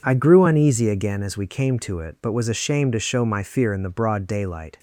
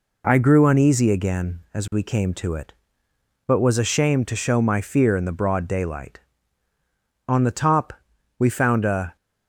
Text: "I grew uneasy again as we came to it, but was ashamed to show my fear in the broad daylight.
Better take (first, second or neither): first